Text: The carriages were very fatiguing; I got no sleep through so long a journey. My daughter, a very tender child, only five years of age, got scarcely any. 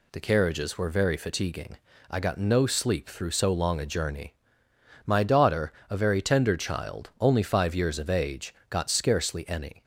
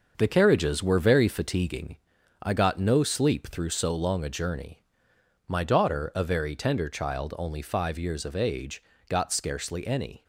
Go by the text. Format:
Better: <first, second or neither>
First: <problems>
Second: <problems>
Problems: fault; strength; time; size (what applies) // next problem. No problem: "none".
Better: first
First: none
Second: gets quieter; throughout; 6 dB